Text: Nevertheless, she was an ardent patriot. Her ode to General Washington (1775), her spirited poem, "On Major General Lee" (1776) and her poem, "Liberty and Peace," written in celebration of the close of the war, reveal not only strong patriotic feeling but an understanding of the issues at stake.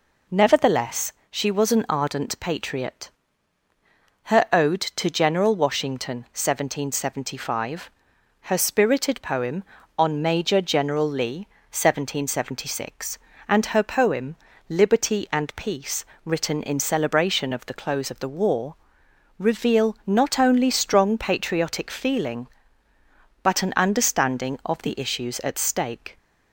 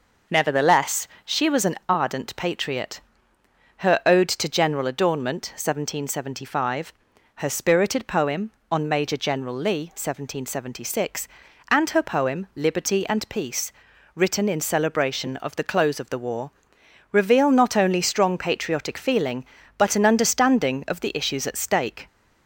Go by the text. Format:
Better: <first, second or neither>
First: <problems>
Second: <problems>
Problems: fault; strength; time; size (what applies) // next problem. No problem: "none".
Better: first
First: none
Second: says "Adornment" for "Washington"; at 4.8 s